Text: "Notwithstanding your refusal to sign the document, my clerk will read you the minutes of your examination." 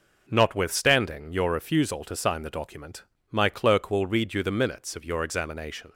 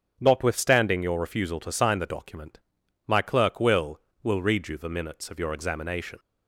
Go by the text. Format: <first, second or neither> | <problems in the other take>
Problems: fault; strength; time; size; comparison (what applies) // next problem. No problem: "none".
first | starts louder than the rest; until 1.2 s; 7 dB // says "will" twice; at 4.2 s